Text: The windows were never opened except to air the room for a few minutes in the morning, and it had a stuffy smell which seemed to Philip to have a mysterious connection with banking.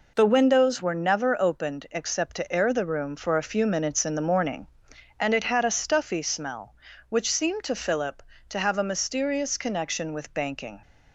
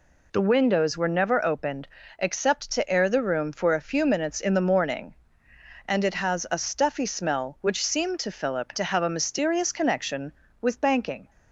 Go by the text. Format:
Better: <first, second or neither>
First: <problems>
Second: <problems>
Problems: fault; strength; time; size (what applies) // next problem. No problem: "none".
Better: first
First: none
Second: pauses between "opened" and "except"; slight; at 1.8 s; 0.32 s long // says "has" for "had"; at 6.1 s